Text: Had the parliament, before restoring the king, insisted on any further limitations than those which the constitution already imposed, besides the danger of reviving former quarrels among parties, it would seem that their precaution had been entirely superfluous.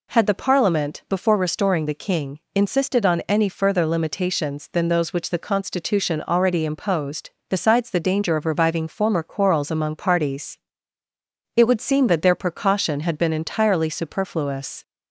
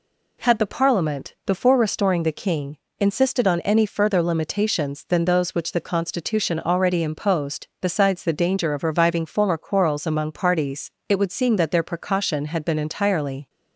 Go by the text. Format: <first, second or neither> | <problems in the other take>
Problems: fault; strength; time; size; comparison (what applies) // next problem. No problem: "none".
first | stops before "superfluous"; at 13.4 s